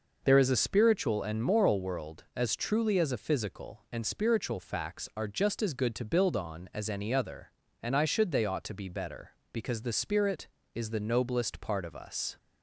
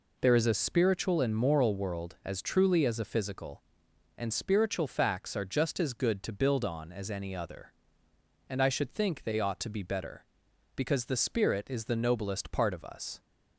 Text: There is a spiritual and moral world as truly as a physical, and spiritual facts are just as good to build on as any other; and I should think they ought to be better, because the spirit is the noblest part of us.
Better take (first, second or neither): second